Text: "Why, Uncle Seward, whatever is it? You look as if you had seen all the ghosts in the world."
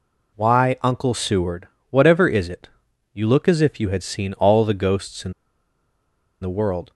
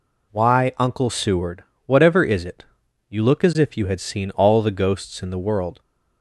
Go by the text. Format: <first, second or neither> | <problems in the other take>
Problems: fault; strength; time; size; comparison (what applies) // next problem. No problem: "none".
second | pauses between "in" and "the"; at 5.3 s; 1.1 s long